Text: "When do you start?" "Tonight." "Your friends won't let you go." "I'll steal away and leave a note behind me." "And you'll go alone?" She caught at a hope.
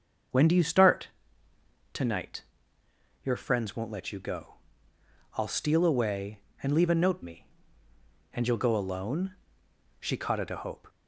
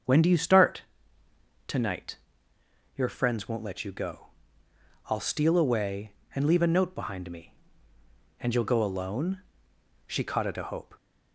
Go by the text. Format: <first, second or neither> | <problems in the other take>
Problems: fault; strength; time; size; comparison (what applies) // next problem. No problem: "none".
second | starts louder than the rest; until 2.1 s; 6.5 dB; also in the second // skips "behind"; at 7.2 s